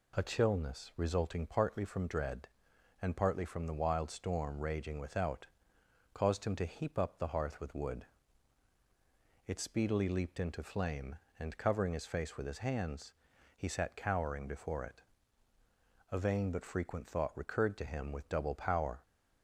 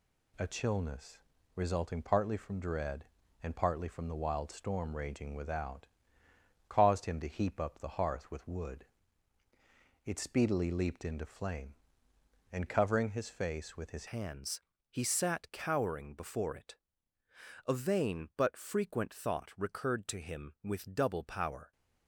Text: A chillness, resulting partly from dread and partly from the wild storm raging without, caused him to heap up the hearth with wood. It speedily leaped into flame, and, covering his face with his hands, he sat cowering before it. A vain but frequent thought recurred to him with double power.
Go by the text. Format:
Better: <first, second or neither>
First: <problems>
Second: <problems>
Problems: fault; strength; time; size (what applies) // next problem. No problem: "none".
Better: first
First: none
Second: changes voice at "hands"; from 14.0 s on; 7.7 s long